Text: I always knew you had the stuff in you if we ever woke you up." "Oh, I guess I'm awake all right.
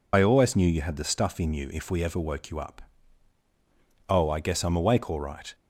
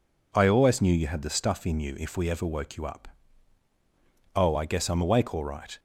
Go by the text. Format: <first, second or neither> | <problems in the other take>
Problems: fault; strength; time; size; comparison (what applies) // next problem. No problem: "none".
second | loses the start of "I"; at 0.1 s; 50 ms